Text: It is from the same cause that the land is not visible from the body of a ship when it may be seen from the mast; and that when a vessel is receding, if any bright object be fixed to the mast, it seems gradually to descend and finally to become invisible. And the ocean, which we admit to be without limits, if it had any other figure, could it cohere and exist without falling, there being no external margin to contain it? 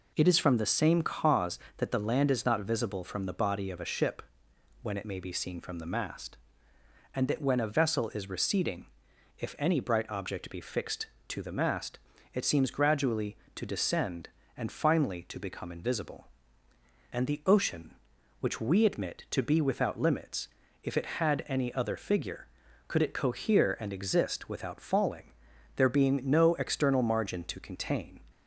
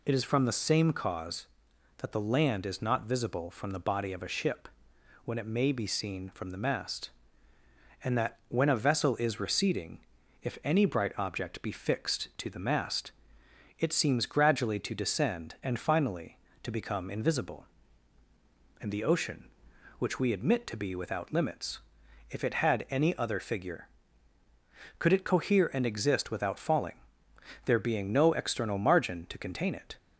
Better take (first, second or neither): second